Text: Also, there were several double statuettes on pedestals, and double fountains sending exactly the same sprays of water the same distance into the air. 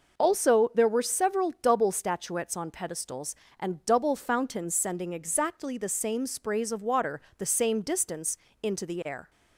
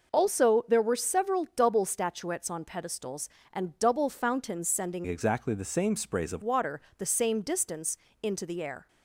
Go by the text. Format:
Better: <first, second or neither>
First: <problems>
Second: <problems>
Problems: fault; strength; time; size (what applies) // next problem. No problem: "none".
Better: first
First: pauses between "water" and "the"; slight; at 7.1 s; 0.18 s long // pauses between "distance" and "into"; slight; at 8.3 s; 0.24 s long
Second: changes voice from "exactly" to "of"; from 5.0 to 6.4 s; 1.4 s long // pauses between "water" and "the"; slight; at 6.7 s; 0.18 s long // pauses between "distance" and "into"; slight; at 7.9 s; 0.24 s long